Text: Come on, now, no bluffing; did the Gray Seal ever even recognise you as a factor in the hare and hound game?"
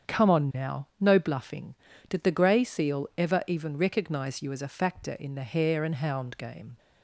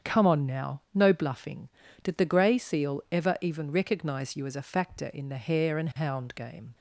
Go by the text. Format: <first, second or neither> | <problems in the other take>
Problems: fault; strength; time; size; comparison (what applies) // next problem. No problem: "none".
neither | starts louder than the rest; strong; the same in both